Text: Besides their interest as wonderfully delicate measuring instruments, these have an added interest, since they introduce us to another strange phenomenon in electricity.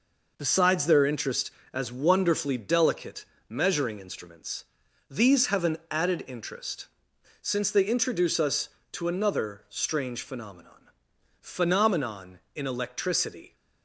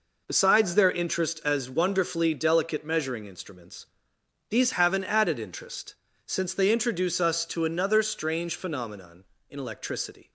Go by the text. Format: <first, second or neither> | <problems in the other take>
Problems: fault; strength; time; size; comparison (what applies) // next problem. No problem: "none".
second | pauses between "delicate" and "measuring"; slight; at 3.2 s; 0.24 s long // says "phenomenon" twice; at 11.4 s